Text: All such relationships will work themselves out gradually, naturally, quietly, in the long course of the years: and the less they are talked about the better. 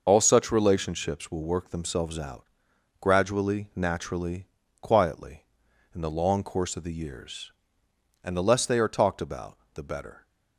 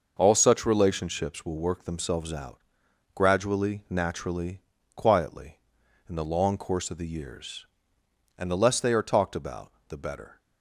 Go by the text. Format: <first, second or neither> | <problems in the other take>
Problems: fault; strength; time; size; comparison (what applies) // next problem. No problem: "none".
second | loses the start of "All"; at 0.0 s; 35 ms // pauses between "out" and "gradually"; noticeable; at 2.4 s; 0.54 s long; noticeable in the second // pauses between "about" and "the"; slight; at 9.5 s; 0.18 s long; slight in the second